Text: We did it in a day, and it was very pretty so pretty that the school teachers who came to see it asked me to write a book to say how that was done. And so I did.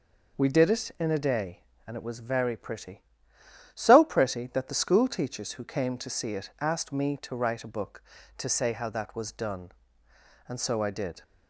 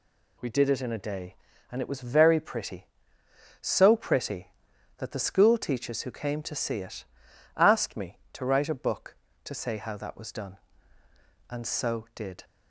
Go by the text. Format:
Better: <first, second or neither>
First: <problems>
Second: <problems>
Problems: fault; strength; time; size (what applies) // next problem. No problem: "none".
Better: first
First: none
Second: pauses between "it" and "asked"; noticeable; at 7.0 s; 0.52 s long // skips "I"; at 12.0 s